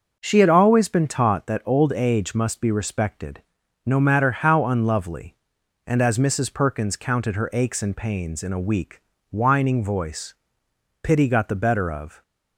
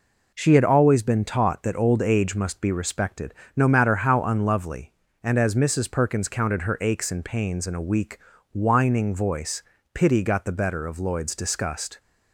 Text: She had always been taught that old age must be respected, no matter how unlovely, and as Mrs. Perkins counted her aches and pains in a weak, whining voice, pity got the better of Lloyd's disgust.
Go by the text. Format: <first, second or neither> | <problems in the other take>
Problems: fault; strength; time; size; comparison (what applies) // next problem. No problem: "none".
second | starts louder than the rest; until 1.2 s; 6.5 dB // stops before "Lloyd's disgust"; at 12.2 s